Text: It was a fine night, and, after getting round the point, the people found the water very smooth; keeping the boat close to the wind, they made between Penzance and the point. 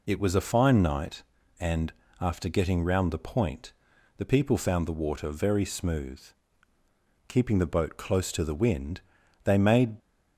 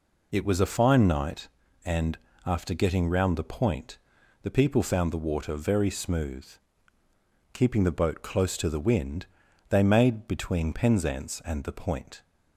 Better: second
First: stops before "between Penzance and the point"; at 10.0 s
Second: none

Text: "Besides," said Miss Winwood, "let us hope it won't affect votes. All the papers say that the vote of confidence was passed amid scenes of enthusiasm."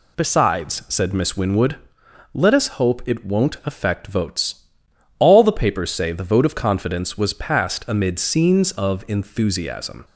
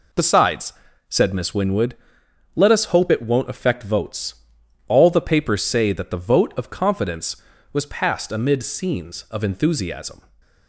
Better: second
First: skips "that"; at 6.1 s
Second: none

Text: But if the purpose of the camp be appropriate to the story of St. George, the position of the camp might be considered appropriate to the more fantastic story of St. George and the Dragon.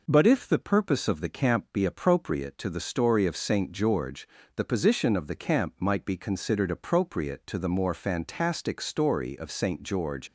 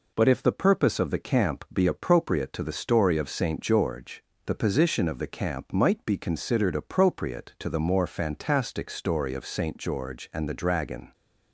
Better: second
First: stops before "and the Dragon"; at 10.2 s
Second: none

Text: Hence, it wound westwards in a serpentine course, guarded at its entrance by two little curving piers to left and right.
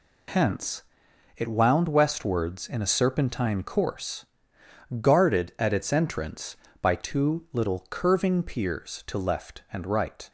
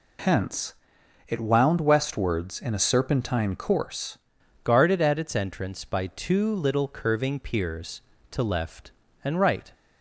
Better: first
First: none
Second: changes voice at "guarded"; from 4.6 s on; 5.1 s long

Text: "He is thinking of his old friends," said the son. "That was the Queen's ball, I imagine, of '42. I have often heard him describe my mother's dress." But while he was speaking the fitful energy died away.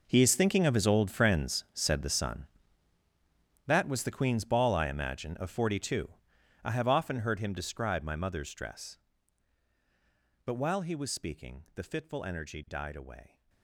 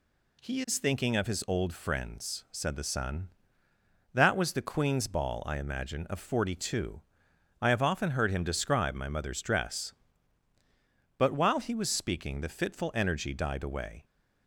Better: second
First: gets quieter; strong; throughout; 15.5 dB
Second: none

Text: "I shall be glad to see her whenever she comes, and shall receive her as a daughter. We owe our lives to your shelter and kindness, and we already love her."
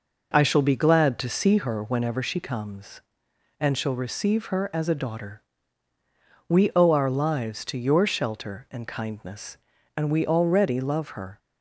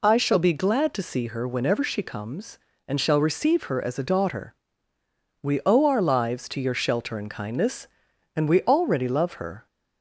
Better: neither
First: none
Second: none

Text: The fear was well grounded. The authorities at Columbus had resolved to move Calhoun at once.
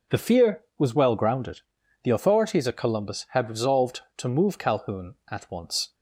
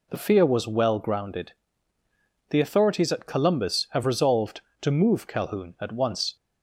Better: first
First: none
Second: says "have" for "had"; at 3.9 s

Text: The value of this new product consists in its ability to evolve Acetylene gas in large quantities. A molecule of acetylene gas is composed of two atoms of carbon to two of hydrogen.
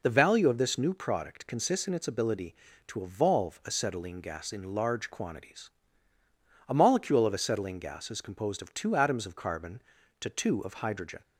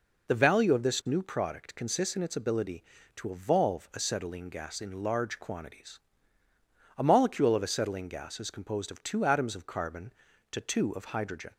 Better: neither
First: none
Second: none

